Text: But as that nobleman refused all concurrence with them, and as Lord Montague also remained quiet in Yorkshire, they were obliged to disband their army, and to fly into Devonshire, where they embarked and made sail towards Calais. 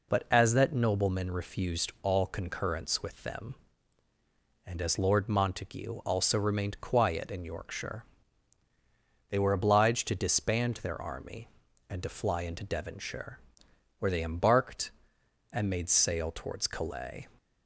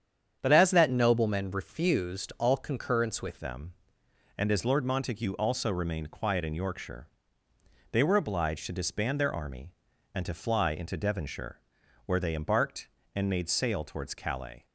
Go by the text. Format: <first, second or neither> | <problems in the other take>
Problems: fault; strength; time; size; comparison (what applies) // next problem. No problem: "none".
first | starts louder than the rest; strong; until 1.4 s; 8.5 dB // changes voice at "them"; from 3.3 s on; 11.3 s long